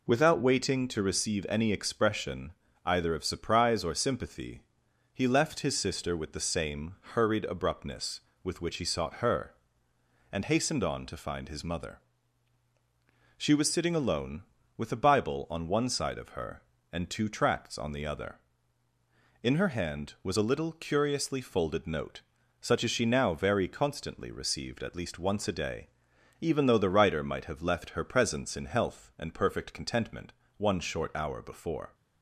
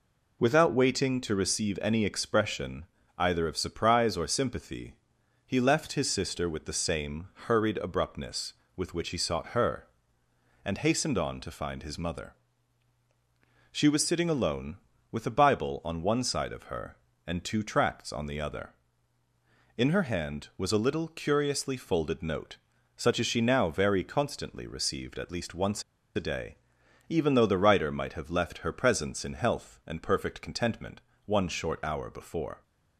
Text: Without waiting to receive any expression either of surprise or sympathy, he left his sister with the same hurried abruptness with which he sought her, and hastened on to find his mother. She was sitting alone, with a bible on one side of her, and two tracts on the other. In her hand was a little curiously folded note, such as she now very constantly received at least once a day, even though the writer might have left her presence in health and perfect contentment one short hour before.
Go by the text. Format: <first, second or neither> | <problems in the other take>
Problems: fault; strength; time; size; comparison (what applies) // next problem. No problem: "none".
first | pauses between "expression" and "either"; slight; at 2.8 s; 0.32 s long; slight in the first // pauses between "same" and "hurried"; slight; at 7.2 s; 0.18 s long; slight in the first // pauses between "once" and "a"; slight; at 25.8 s; 0.33 s long // pauses between "contentment" and "one"; slight; at 31.0 s; 0.26 s long; slight in the first